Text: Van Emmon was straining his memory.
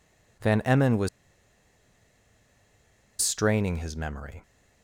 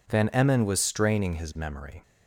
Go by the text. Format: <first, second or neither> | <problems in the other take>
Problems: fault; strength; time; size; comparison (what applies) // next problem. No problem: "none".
second | pauses between "was" and "straining"; strong; at 1.0 s; 2.1 s long